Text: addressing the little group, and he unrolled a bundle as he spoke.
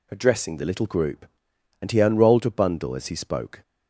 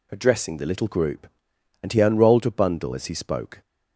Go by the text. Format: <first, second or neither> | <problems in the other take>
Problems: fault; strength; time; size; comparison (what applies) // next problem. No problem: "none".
neither | none